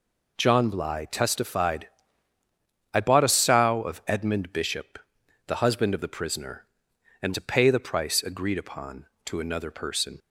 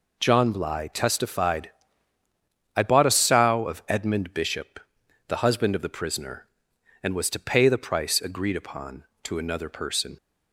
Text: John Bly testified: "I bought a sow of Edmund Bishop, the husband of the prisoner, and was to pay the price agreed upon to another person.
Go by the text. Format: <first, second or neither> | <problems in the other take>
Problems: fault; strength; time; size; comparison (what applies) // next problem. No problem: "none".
second | skips "was"; at 7.3 s